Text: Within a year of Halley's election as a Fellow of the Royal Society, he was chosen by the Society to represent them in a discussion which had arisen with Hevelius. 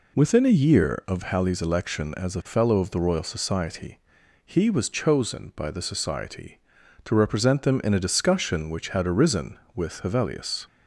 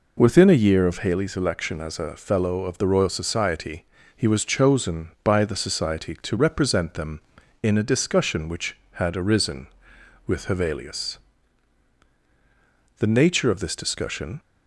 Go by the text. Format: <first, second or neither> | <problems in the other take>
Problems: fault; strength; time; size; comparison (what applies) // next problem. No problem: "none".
first | goes on to say "The nature of this discussion"; from 12.9 s on; 1.4 s long